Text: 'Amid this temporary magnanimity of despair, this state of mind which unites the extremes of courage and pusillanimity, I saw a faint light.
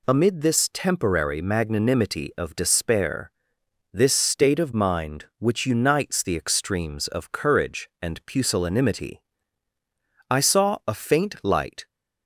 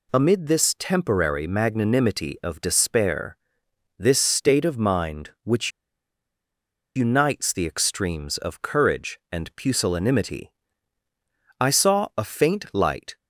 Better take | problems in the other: first | pauses between "which" and "unites"; strong; at 5.6 s; 1.2 s long

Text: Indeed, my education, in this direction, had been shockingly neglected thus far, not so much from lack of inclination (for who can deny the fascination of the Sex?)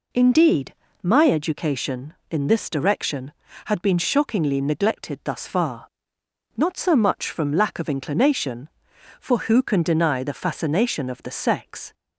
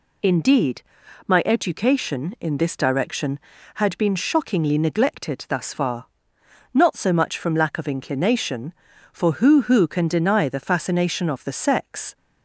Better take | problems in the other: first | says "who" twice; at 9.6 s

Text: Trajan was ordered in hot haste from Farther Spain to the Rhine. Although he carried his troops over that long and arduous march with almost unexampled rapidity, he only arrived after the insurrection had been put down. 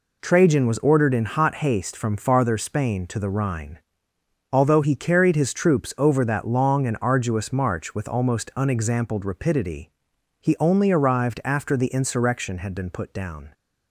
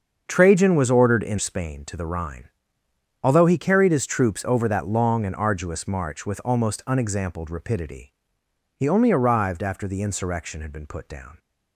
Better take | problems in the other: first | starts louder than the rest; until 1.2 s; 6.5 dB // skips "hot haste from Farther"; at 1.3 s

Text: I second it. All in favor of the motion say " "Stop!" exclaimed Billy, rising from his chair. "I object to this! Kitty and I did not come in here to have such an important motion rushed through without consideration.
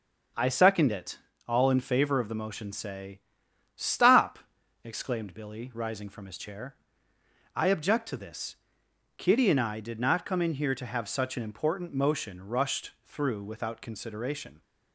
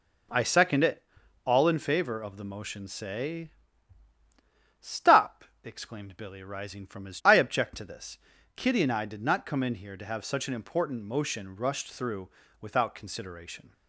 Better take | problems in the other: first | skips "chair"; at 7.2 s // pauses between "through" and "without"; slight; at 12.2 s; 0.32 s long

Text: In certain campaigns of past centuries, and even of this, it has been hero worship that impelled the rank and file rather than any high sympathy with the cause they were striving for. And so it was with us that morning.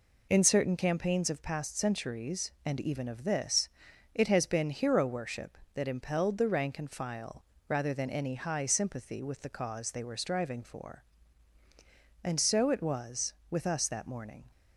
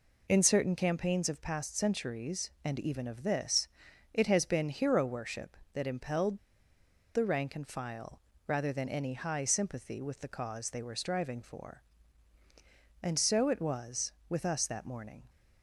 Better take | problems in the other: first | pauses between "impelled" and "the"; noticeable; at 6.3 s; 0.77 s long // pauses between "file" and "rather"; slight; at 8.1 s; 0.28 s long; slight in the first

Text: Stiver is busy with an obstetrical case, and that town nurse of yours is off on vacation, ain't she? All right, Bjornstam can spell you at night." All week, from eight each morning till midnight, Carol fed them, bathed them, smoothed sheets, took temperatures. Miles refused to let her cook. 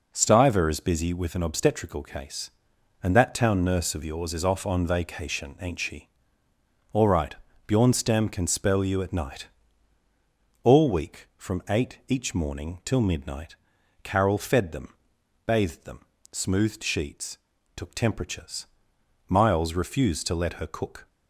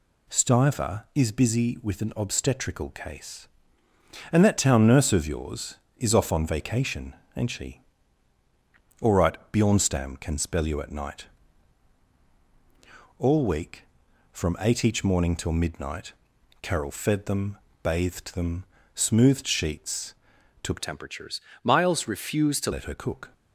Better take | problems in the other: first | changes voice from "temperatures" to "to"; from 20.7 to 22.7 s; 2.0 s long

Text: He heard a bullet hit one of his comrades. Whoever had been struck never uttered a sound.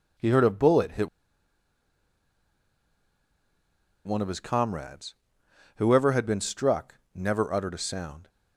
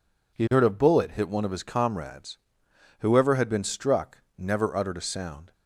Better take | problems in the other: second | pauses between "hit" and "one"; strong; at 1.0 s; 2.9 s long // pauses between "struck" and "never"; slight; at 6.9 s; 0.16 s long; slight in the second

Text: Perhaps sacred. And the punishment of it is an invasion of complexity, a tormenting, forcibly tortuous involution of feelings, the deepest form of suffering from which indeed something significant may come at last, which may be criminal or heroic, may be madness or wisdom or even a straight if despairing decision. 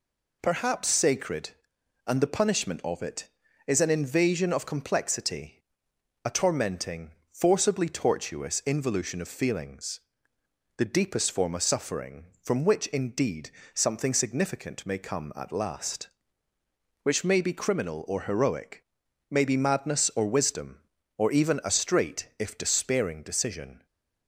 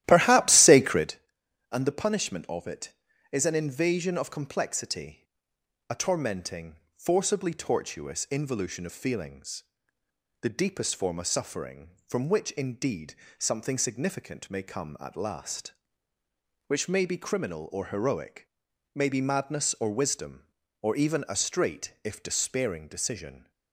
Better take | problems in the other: first | starts louder than the rest; strong; until 1.2 s; 14 dB // pauses between "indeed" and "something"; slight; at 13.1 s; 0.24 s long; slight in the first

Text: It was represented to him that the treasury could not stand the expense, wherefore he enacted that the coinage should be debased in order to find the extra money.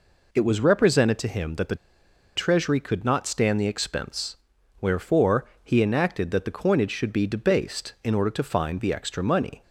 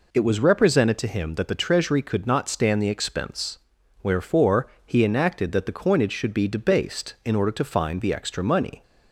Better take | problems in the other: second | pauses between "the" and "treasury"; noticeable; at 1.7 s; 0.60 s long // pauses between "wherefore" and "he"; slight; at 5.4 s; 0.16 s long; slight in the second

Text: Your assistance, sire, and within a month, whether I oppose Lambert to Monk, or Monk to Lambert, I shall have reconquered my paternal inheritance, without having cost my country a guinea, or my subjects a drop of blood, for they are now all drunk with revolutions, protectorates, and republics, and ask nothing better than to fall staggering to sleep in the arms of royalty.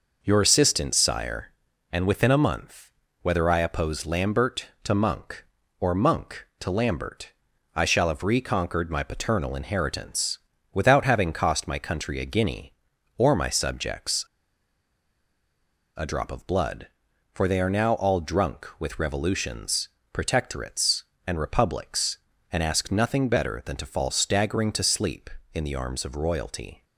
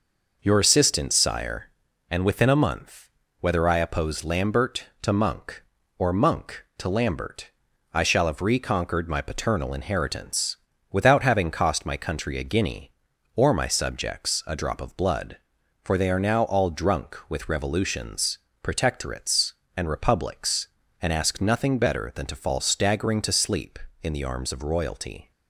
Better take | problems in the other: second | pauses between "subjects" and "a"; strong; at 14.2 s; 1.7 s long

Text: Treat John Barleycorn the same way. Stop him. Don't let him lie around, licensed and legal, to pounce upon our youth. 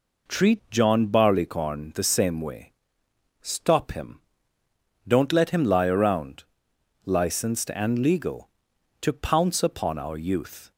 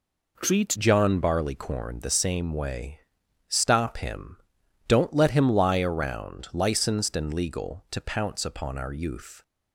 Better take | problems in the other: first | changes voice at "John"; from 0.7 s on; 8.7 s long

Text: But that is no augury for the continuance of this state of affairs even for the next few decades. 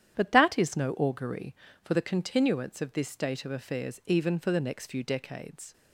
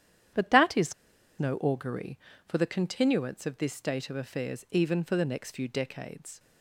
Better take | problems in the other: first | starts louder than the rest; strong; until 1.8 s; 10 dB; strong in the first // pauses between "is" and "no"; noticeable; at 0.9 s; 0.47 s long

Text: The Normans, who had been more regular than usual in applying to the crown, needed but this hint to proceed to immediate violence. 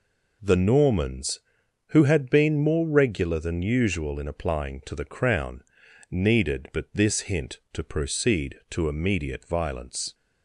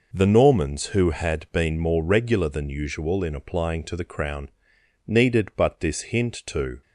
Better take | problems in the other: first | stops before "proceed to immediate violence"; at 6.8 s

